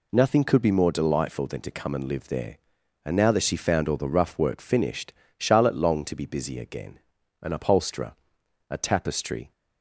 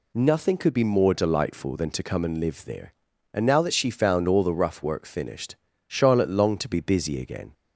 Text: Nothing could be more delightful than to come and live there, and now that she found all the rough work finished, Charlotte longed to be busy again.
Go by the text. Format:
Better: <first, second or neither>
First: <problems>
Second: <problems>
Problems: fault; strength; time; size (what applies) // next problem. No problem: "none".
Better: second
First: goes on to say "An upholsterer a tapestry"; strong; from 7.4 s on; 2.1 s long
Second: none